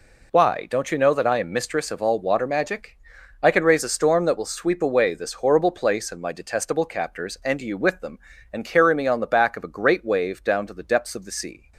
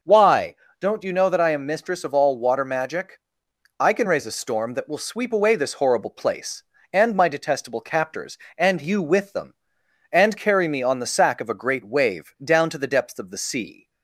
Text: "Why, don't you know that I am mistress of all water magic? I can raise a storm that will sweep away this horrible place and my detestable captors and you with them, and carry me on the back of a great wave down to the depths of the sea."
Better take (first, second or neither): first